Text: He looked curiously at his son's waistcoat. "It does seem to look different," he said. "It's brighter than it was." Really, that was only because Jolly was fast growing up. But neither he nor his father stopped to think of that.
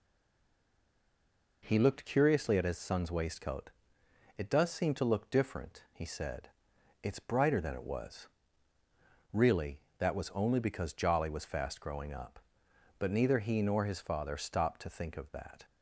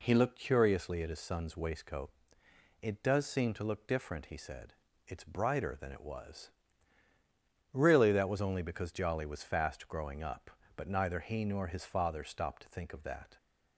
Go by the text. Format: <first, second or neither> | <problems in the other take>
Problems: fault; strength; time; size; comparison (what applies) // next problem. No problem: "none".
second | stays silent before the first word; noticeable; until 1.6 s; 1.6 s long